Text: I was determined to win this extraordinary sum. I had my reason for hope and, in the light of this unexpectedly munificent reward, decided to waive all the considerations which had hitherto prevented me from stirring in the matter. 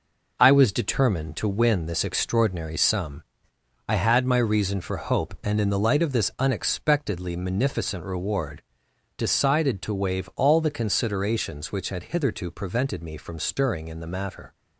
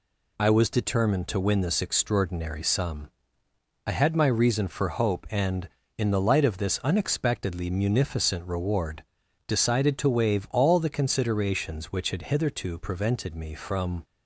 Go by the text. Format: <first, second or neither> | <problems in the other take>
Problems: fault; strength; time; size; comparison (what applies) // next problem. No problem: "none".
first | stops before "stirring in the matter"; at 14.0 s